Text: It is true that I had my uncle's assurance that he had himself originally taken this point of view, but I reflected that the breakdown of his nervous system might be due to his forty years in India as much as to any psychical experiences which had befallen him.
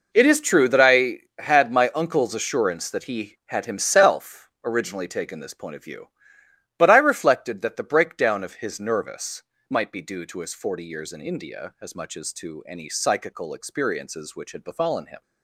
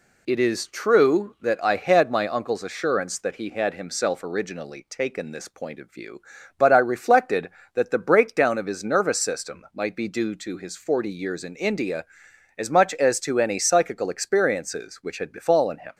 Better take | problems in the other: second | skips "system"; at 9.5 s

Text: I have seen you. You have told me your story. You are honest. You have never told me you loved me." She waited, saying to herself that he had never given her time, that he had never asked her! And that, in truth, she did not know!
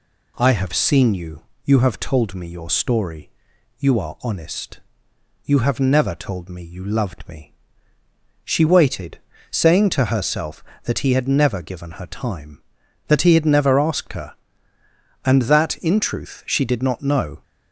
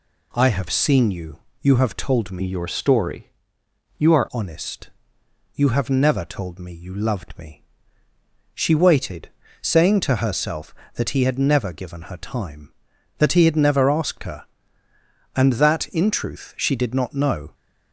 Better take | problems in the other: first | changes voice from "your" to "are"; from 2.4 to 4.2 s; 1.8 s long

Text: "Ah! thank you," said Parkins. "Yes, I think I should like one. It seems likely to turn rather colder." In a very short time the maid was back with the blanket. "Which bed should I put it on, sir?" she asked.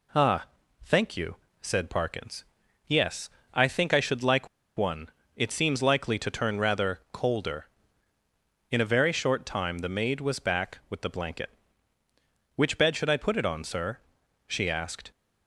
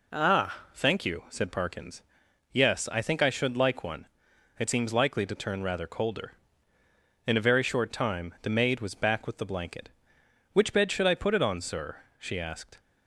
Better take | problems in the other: second | pauses between "like" and "one"; slight; at 4.4 s; 0.29 s long

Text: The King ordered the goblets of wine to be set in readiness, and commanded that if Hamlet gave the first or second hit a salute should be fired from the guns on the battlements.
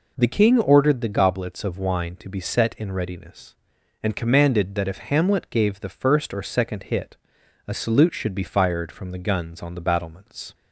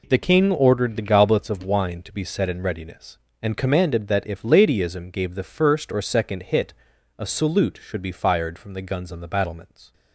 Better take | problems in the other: first | says "Ladyism" for "Hamlet"; at 4.4 s // pauses between "hit" and "a"; at 6.7 s; 0.42 s long; noticeable in the first

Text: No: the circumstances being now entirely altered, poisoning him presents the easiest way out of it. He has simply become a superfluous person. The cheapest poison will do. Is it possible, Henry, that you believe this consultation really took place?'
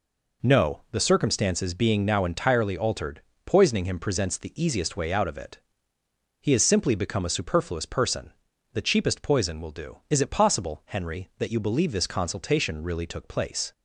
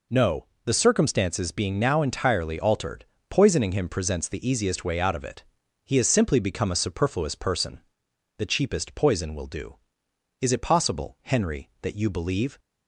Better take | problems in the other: first | stops before "this consultation really took place"; at 12.5 s

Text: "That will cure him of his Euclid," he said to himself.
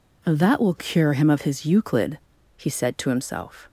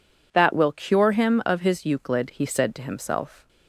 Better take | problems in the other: neither | none

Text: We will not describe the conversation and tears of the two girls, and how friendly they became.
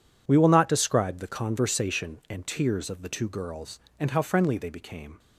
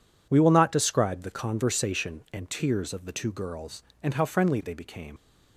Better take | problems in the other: first | leaves "became" unfinished; at 5.1 s; 65 ms

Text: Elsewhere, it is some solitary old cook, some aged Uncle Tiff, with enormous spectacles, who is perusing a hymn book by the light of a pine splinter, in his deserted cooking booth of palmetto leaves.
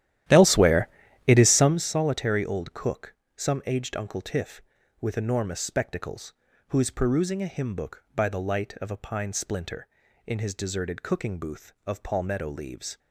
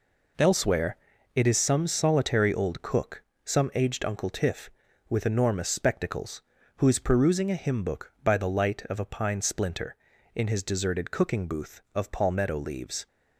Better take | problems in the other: second | starts louder than the rest; strong; until 1.9 s; 12.5 dB

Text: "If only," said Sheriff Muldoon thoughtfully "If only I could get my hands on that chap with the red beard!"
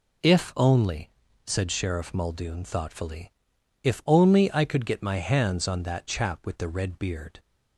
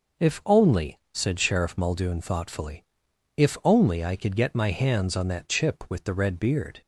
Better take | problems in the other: first | pauses between "thoughtfully" and "If"; noticeable; at 2.8 s; 0.54 s long; noticeable in the first // says "chip" for "chap"; at 5.4 s

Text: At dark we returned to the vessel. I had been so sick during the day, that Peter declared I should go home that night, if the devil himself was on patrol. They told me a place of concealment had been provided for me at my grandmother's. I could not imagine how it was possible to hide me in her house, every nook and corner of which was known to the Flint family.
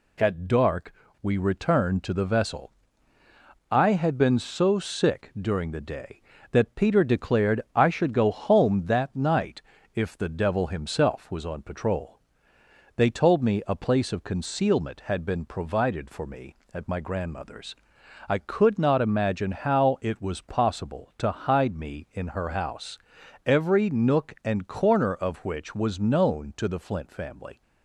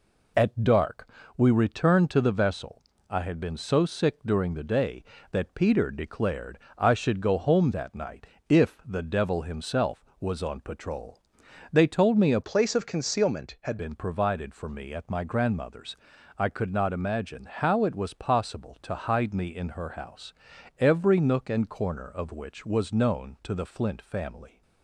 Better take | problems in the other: first | pauses between "dark" and "we"; slight; at 1.0 s; 0.28 s long; slight in the first // pauses between "declared" and "I"; slight; at 6.5 s; 0.18 s long // changes voice from "place" to "had"; from 12.4 to 13.7 s; 1.3 s long

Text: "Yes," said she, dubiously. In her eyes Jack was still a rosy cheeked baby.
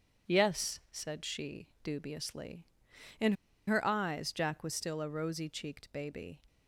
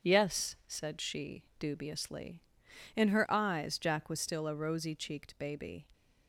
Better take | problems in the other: second | pauses between "In" and "her"; slight; at 3.3 s; 0.34 s long

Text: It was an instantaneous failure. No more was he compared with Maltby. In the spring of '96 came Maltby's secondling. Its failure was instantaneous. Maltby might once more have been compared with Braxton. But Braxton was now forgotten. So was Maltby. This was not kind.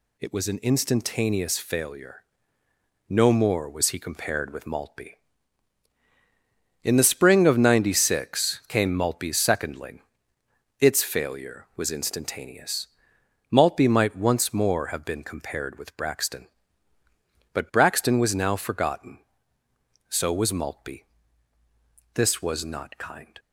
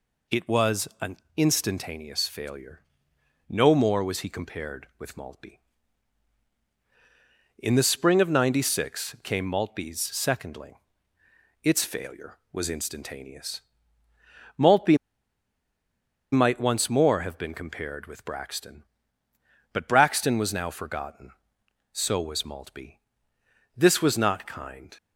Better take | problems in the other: first | pauses between "an" and "instantaneous"; slight; at 1.1 s; 0.18 s long // pauses between "Maltby" and "might"; strong; at 14.9 s; 1.3 s long

